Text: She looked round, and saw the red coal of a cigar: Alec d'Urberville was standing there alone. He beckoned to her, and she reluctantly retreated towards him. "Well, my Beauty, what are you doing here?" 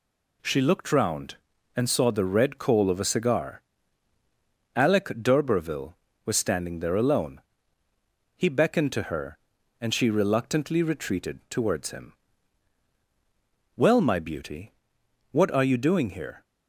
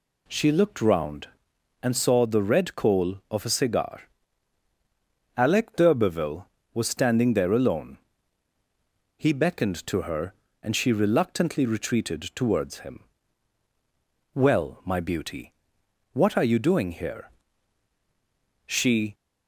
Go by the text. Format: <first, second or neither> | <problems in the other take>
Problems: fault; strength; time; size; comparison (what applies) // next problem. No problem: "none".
first | goes on to say "She"; slight; from 18.6 s on; 0.48 s long